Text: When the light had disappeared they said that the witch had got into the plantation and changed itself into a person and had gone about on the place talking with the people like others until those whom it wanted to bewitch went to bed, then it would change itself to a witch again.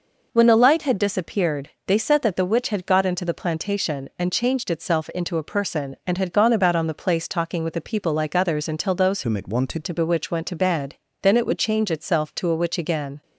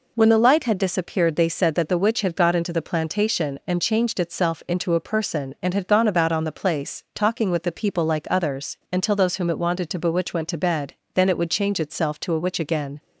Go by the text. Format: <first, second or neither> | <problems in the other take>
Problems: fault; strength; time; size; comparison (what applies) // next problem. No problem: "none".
second | pauses between "disappeared" and "they"; slight; at 1.6 s; 0.18 s long // changes voice from "whom" to "wanted"; from 9.2 to 9.8 s; 0.6 s long